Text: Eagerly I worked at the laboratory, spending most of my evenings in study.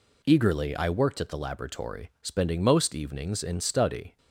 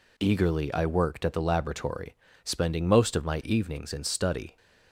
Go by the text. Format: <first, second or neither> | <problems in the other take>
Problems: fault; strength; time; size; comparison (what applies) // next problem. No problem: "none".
second | skips "of my"; at 2.9 s